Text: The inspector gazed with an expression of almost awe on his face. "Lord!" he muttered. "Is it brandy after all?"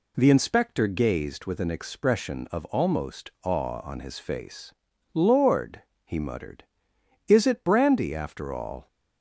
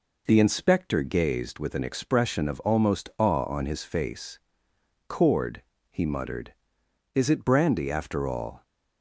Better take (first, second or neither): first